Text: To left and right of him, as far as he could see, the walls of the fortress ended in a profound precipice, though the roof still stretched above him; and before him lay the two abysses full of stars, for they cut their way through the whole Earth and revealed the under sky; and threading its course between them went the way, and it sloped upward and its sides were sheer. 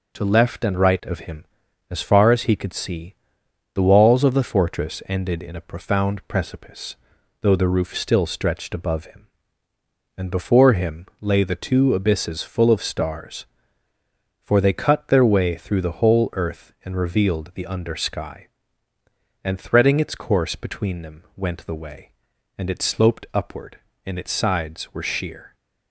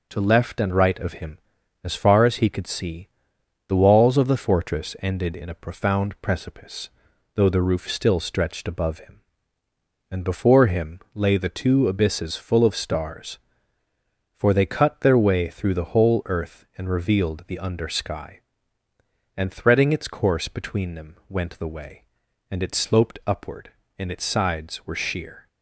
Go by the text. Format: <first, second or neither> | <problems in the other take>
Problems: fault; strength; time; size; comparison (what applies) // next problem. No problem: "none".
neither | none